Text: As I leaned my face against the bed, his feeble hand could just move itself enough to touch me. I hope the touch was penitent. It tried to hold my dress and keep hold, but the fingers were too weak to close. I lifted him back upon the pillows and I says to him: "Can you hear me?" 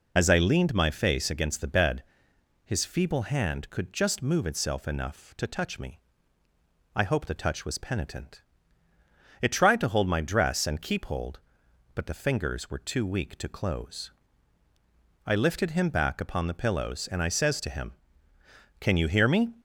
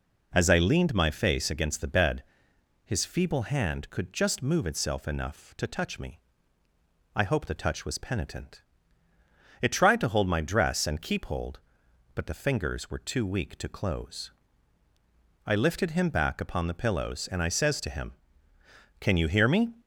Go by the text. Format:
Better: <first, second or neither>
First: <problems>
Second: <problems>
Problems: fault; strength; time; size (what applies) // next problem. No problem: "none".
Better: second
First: loses the start of "As"; at 0.1 s; 35 ms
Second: none